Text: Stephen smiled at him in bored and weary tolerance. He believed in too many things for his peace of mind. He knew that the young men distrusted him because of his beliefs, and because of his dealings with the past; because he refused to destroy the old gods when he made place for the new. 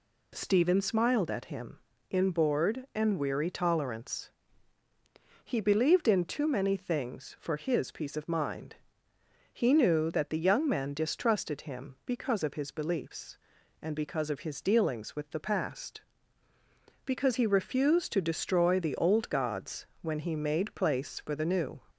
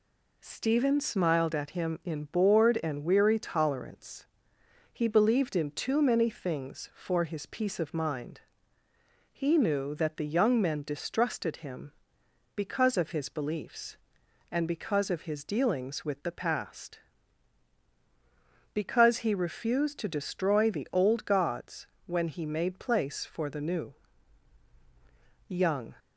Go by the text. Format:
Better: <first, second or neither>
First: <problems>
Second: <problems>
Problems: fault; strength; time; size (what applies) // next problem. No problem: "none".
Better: first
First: pauses between "gods" and "when"; slight; at 19.8 s; 0.16 s long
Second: pauses between "gods" and "when"; slight; at 21.8 s; 0.18 s long // goes on to say "Young"; slight; from 25.4 s on; 0.46 s long